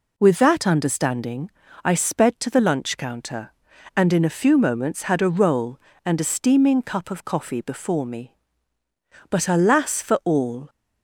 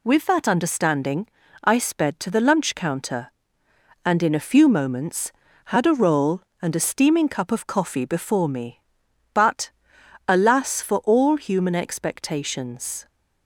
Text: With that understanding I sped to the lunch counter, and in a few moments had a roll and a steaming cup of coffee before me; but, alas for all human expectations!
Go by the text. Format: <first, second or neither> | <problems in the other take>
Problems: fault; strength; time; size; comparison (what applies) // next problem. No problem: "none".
second | pauses between "understanding" and "I"; slight; at 1.5 s; 0.34 s long; also in the second // stops before "human expectations"; at 10.6 s